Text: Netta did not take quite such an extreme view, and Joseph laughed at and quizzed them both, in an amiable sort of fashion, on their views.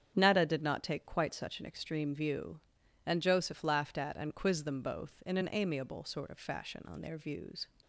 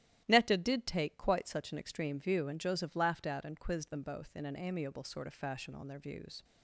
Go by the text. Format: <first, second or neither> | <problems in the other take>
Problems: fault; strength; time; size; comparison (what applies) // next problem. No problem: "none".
first | starts louder than the rest; strong; until 1.2 s; 12.5 dB; strong in the first // skips "not"; at 0.8 s